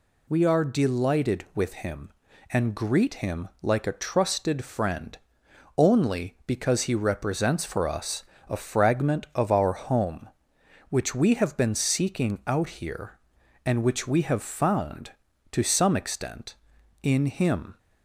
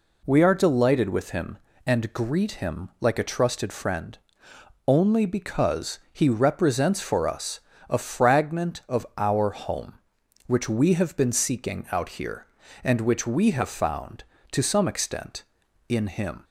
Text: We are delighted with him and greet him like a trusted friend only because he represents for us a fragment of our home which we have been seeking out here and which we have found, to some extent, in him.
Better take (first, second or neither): neither